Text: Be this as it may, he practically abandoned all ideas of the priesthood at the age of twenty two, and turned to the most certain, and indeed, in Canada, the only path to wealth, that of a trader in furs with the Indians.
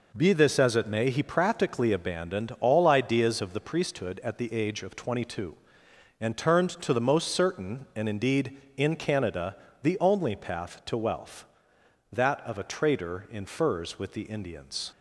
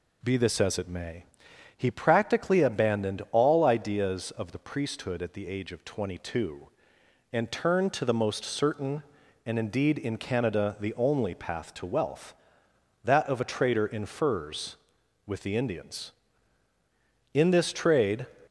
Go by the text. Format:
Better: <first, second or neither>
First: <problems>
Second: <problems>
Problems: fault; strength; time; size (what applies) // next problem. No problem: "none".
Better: first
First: none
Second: goes on to say "In this trade"; noticeable; from 17.3 s on; 0.94 s long